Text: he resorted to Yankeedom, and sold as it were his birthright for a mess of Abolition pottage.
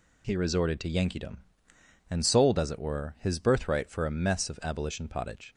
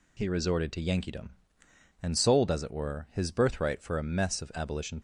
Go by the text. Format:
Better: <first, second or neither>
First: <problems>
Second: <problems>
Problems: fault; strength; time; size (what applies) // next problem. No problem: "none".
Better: first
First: none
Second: stops before "pottage"; at 4.9 s